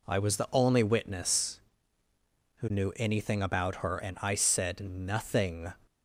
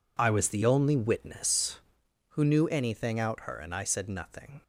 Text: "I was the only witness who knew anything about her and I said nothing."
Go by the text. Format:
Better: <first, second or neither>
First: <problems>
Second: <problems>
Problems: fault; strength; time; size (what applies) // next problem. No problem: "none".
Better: first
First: none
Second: says "out" for "about"; at 3.1 s